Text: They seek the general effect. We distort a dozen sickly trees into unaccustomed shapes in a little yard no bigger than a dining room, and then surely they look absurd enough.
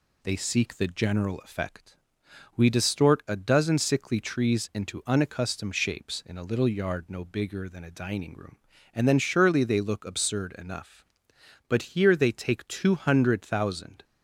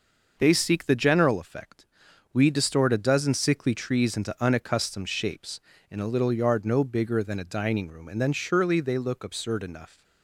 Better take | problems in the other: second | goes on to say "But here they take two hundred thousand"; strong; from 11.6 s on; 2.3 s long

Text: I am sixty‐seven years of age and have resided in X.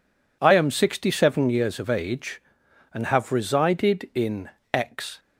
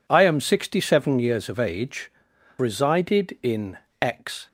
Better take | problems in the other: first | skips "and have"; at 2.3 s // pauses between "in" and "X"; slight; at 3.7 s; 0.24 s long; slight in the first

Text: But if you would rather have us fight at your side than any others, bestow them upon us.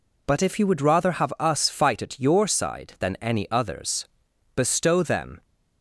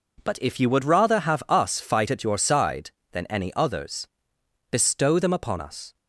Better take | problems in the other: second | stops before "upon us"; at 5.4 s

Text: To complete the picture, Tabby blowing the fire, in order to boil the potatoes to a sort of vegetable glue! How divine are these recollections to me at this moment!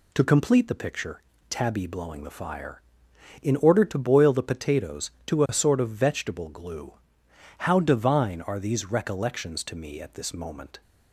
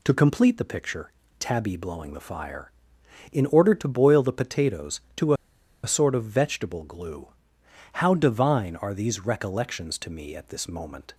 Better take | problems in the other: first | pauses between "to" and "a"; noticeable; at 5.3 s; 0.50 s long

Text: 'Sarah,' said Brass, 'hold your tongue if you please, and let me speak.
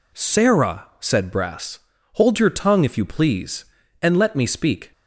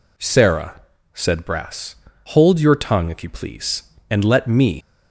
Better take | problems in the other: first | stops before "speak"; at 4.8 s

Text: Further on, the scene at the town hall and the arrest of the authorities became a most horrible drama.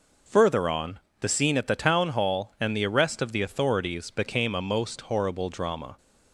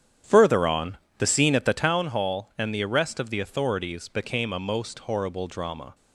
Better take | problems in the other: first | starts louder than the rest; strong; until 1.8 s; 9.5 dB

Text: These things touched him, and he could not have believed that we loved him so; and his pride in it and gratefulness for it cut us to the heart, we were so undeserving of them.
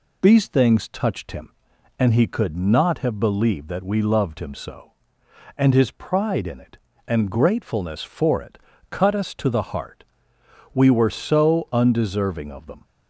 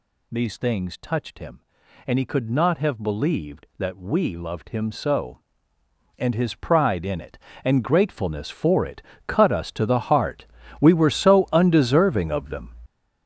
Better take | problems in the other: first | gets louder; strong; throughout; 10 dB // pauses between "it" and "cut"; slight; at 9.0 s; 0.24 s long; slight in the first

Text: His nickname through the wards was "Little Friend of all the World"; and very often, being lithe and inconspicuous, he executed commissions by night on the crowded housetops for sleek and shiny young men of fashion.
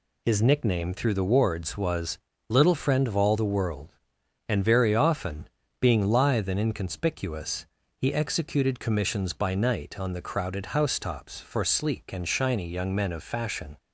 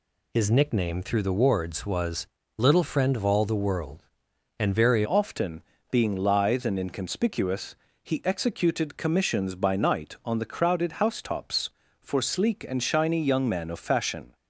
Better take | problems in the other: first | pauses between "was" and "Little"; slight; at 2.2 s; 0.32 s long; slight in the first // changes voice at "often"; from 5.0 s on; 9.3 s long

